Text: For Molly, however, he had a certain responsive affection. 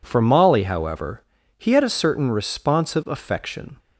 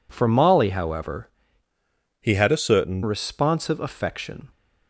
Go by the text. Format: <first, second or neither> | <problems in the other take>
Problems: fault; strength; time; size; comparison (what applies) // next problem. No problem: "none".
first | changes voice from "he" to "certain"; from 2.1 to 3.0 s; 0.9 s long